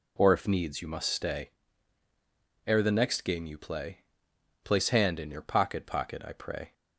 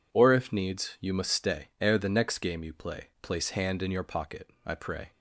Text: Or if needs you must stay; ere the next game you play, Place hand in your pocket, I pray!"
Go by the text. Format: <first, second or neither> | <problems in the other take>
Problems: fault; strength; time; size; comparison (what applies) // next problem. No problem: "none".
second | says "pocket" twice; at 5.8 s